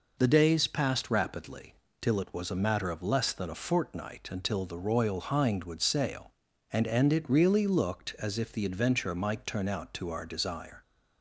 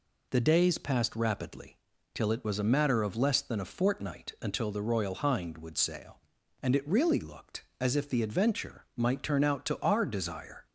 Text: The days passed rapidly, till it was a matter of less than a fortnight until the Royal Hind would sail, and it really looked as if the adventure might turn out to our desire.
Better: second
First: says "and" twice; at 6.8 s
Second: none

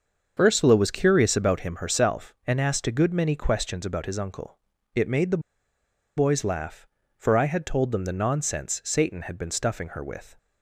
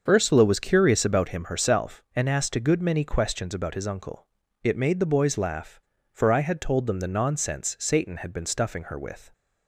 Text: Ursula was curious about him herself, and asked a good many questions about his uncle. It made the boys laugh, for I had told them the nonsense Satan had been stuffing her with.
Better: second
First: starts louder than the rest; until 1.4 s; 6.5 dB // pauses between "the" and "boys"; noticeable; at 5.4 s; 0.77 s long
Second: starts louder than the rest; until 1.0 s; 6.5 dB

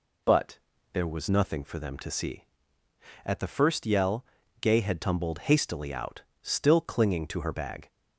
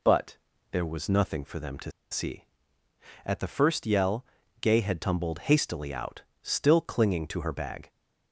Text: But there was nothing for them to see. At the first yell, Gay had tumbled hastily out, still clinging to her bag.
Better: first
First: pauses between "But" and "there"; slight; at 0.5 s; 0.34 s long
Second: pauses between "But" and "there"; slight; at 0.3 s; 0.34 s long // pauses between "to" and "see"; slight; at 1.9 s; 0.19 s long

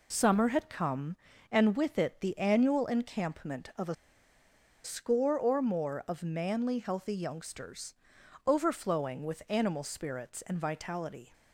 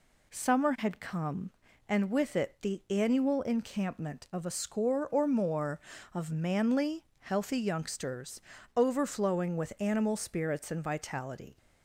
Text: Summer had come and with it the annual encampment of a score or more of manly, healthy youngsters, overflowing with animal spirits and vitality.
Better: second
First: pauses between "a" and "score"; noticeable; at 3.9 s; 0.89 s long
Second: none

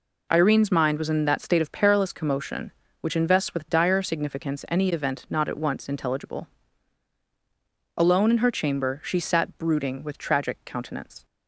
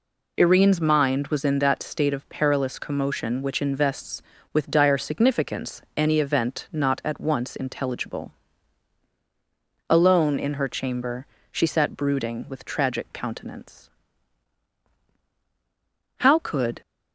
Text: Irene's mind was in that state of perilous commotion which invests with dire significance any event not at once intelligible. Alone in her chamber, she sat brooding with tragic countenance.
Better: first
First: none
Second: goes on to say "How could"; noticeable; from 16.1 s on; 0.64 s long

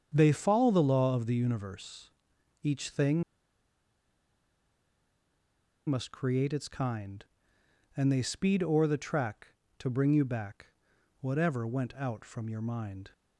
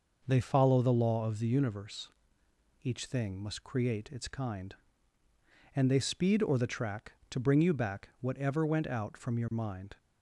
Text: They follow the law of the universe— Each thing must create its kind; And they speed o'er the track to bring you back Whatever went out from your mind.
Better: second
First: starts louder than the rest; strong; until 1.1 s; 7.5 dB // pauses between "thing" and "must"; strong; at 3.2 s; 2.6 s long // pauses between "back" and "Whatever"; noticeable; at 10.6 s; 0.54 s long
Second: none

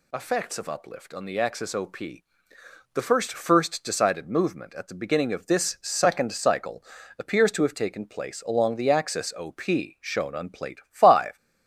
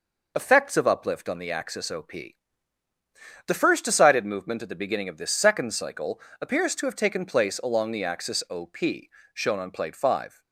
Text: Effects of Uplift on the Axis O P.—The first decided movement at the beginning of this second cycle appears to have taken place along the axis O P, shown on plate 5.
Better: second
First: says "first" twice; at 3.3 s // pauses between "cycle" and "appears"; slight; at 6.8 s; 0.36 s long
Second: pauses between "cycle" and "appears"; slight; at 6.2 s; 0.18 s long

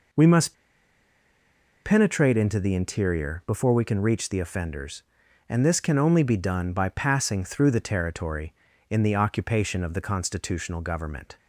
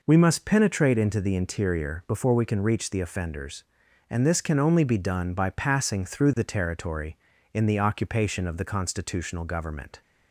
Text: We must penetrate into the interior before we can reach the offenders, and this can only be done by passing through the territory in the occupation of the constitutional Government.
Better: second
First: pauses between "must" and "penetrate"; strong; at 0.5 s; 1.2 s long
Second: none

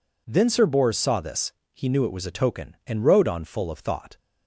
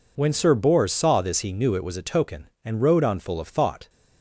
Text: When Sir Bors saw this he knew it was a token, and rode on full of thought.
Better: second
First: says "Then" for "When"; at 0.2 s // pauses between "this" and "he"; slight; at 1.5 s; 0.22 s long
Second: none

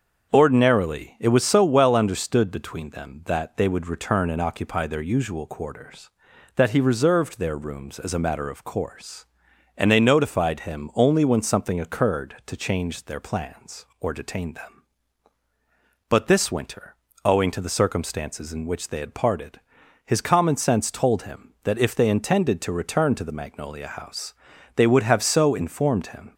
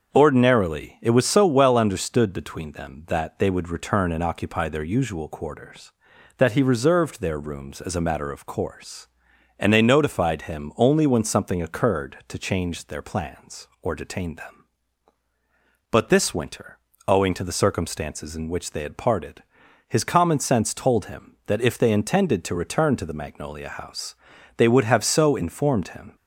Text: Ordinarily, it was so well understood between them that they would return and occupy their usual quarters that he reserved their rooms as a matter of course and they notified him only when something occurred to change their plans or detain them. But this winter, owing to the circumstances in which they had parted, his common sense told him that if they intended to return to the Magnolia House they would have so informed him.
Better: neither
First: starts louder than the rest; until 1.3 s; 6.5 dB // pauses between "House" and "they"; at 24.3 s; 0.42 s long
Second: starts louder than the rest; until 1.1 s; 6.5 dB // pauses between "House" and "they"; at 24.1 s; 0.42 s long

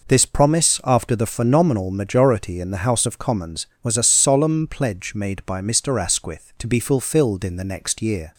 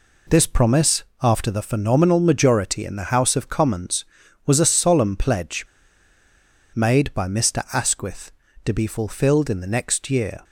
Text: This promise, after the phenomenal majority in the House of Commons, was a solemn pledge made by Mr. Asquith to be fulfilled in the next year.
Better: first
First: none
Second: pauses between "pledge" and "made"; at 5.6 s; 1.1 s long

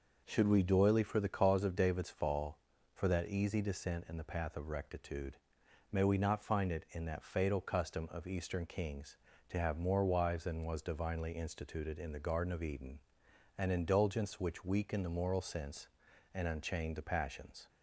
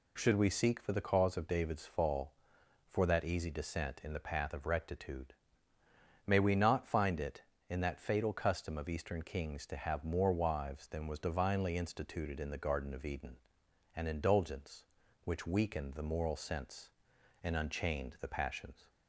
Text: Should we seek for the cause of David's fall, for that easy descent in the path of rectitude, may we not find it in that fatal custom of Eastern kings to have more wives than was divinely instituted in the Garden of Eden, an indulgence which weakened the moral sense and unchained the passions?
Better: second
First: says "doily" for "seek"; at 0.6 s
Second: none

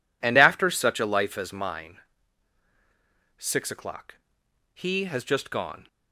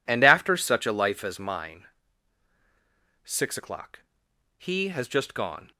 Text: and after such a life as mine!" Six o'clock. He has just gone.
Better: neither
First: none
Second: none

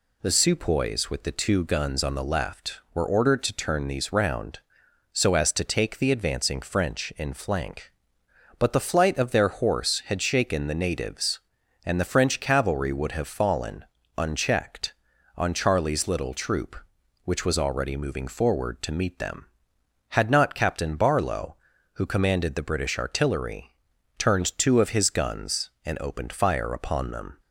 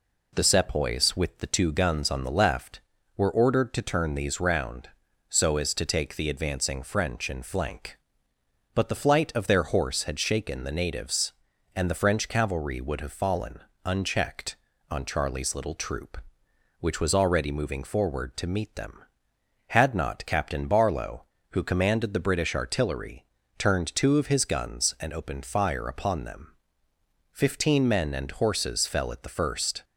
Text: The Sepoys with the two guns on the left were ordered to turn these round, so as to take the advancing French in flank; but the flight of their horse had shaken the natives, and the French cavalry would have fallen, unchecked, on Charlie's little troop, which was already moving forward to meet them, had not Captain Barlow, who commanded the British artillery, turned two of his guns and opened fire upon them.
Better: first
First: none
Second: goes on to say "Fifteen men and horses fell at the first"; strong; from 27.3 s on; 2.5 s long

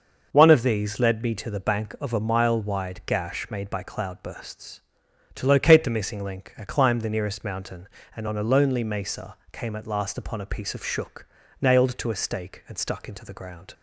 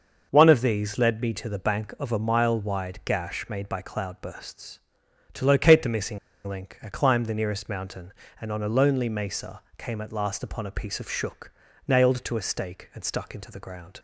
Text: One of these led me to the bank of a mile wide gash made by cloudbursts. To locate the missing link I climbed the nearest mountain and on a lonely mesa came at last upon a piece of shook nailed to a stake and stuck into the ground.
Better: first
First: starts louder than the rest; noticeable; until 1.3 s; 6 dB // pauses between "mesa" and "came"; slight; at 9.3 s; 0.16 s long // pauses between "shook" and "nailed"; at 11.2 s; 0.37 s long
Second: starts louder than the rest; noticeable; until 1.3 s; 6 dB // pauses between "missing" and "link"; slight; at 6.1 s; 0.28 s long // pauses between "mesa" and "came"; slight; at 9.6 s; 0.16 s long // pauses between "shook" and "nailed"; at 11.5 s; 0.38 s long

